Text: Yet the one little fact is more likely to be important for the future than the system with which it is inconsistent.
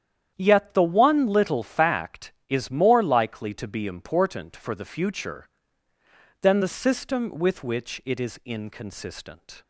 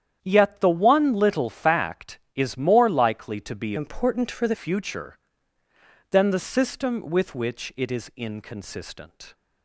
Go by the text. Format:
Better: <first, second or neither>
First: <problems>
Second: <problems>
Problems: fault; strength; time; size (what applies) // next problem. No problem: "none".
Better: first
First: starts louder than the rest; strong; until 1.3 s; 9.5 dB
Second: starts louder than the rest; strong; until 1.2 s; 9.5 dB // changes voice from "important" to "the"; from 3.7 to 4.5 s; 0.8 s long